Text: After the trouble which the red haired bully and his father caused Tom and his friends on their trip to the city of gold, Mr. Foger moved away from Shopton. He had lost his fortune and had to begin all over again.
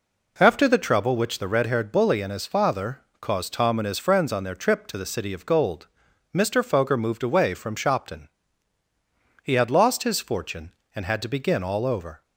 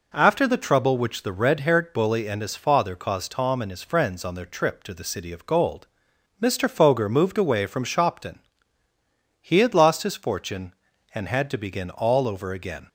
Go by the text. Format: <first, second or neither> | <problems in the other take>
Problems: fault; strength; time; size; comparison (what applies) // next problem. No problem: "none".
second | pauses between "father" and "caused"; slight; at 3.0 s; 0.20 s long // stops before "again"; at 12.2 s